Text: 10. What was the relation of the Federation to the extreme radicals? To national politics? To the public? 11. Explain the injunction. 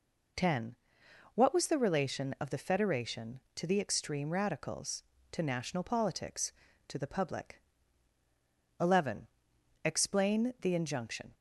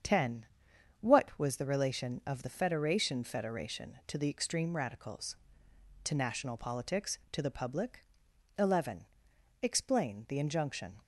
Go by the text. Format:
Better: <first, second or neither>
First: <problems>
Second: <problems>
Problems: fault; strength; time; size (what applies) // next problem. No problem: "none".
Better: first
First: none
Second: starts louder than the rest; strong; until 1.6 s; 7.5 dB // says "Federation" twice; at 3.2 s